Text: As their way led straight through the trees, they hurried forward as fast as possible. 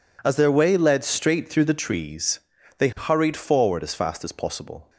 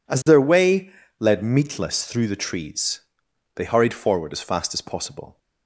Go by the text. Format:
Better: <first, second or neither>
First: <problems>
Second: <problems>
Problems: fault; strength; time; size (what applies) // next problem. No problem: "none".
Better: first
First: none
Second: pauses between "way" and "led"; slight; at 0.8 s; 0.30 s long // says "meatless" for "straight"; at 1.4 s